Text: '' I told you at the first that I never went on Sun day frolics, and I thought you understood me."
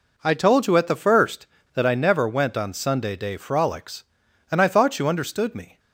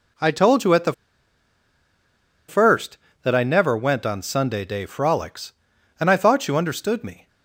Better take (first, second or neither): first